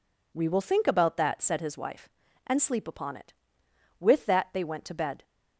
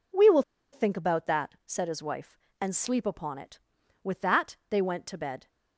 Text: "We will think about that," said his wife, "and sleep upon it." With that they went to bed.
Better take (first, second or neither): first